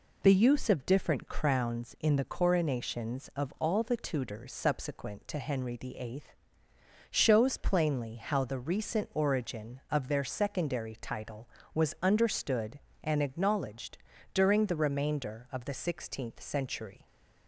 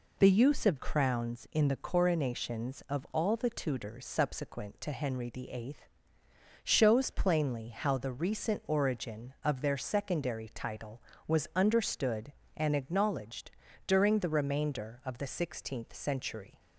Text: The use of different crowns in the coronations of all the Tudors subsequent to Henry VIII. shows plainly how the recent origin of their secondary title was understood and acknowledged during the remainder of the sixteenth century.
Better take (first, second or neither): first